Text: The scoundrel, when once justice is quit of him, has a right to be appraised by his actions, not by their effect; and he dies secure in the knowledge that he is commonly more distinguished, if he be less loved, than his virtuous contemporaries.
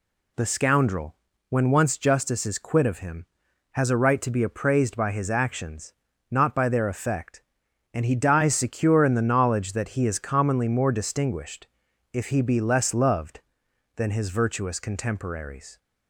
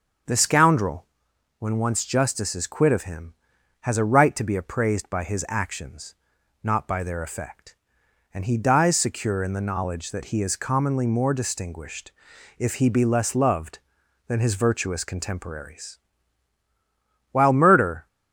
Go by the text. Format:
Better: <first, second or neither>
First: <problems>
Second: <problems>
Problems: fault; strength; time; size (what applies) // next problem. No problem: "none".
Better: first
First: none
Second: starts louder than the rest; until 1.8 s; 6.5 dB // goes on to say "While murder"; noticeable; from 17.2 s on; 0.78 s long